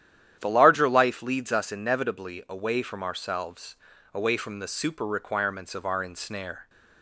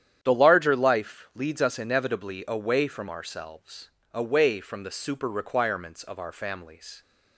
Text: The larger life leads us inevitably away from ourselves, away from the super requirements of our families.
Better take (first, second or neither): second